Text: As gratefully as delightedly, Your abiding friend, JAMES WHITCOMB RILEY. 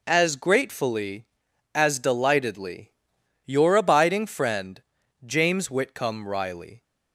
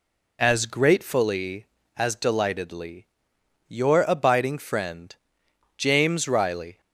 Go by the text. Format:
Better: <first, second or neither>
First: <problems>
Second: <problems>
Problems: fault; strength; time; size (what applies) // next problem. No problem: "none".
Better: first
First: none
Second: skips "WHITCOMB"; at 6.2 s